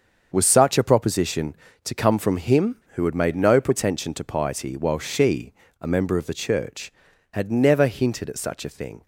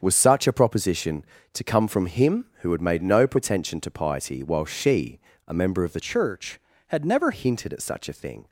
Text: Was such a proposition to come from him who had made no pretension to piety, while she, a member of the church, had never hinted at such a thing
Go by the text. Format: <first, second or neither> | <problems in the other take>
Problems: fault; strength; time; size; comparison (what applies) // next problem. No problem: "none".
first | starts louder than the rest; strong; until 1.0 s; 7 dB; also in the first // changes voice from "church" to "never"; from 5.9 to 7.3 s; 1.4 s long